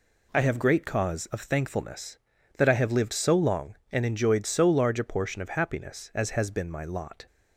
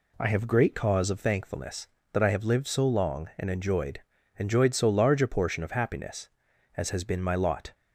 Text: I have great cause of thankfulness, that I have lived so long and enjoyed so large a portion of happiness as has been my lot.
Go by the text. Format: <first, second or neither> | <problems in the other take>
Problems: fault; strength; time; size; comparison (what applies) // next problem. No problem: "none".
first | says "enjoyed" twice; at 4.3 s